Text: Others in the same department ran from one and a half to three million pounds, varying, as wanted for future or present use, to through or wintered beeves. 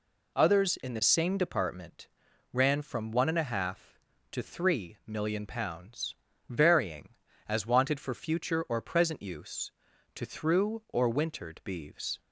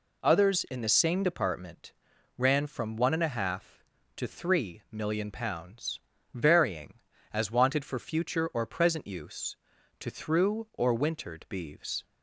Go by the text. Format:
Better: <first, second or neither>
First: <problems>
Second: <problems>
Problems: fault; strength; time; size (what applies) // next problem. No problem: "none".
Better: neither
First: pauses between "department" and "ran"; noticeable; at 2.0 s; 0.46 s long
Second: pauses between "department" and "ran"; noticeable; at 1.9 s; 0.46 s long